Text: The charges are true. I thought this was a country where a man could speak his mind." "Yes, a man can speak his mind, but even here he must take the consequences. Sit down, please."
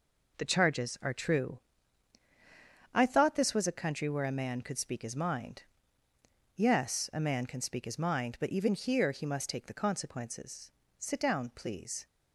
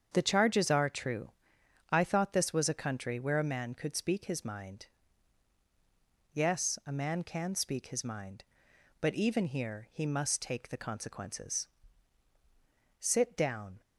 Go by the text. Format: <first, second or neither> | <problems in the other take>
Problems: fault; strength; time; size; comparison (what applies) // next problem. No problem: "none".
first | starts louder than the rest; strong; until 1.1 s; 7.5 dB // stops before "please"; at 13.8 s